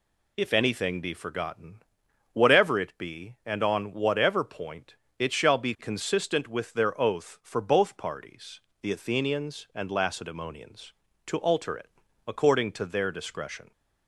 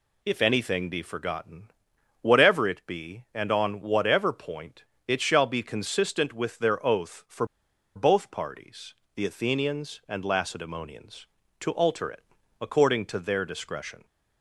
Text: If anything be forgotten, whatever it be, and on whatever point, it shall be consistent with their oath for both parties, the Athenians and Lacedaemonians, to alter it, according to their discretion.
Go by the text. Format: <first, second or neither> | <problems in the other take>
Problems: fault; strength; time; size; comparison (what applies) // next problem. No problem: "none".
first | pauses between "for" and "both"; noticeable; at 7.4 s; 0.51 s long